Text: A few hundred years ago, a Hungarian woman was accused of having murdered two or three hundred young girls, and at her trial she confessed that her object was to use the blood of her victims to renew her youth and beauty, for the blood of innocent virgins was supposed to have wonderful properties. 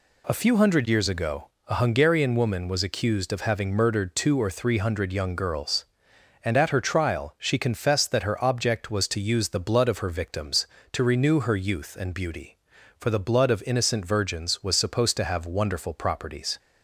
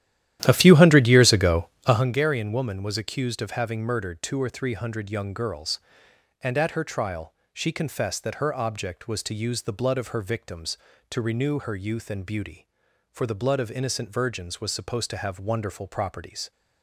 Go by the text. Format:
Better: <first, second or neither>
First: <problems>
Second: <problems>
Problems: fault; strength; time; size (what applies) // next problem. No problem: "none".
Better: first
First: none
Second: starts louder than the rest; strong; until 2.1 s; 12.5 dB // pauses between "trial" and "she"; slight; at 7.3 s; 0.18 s long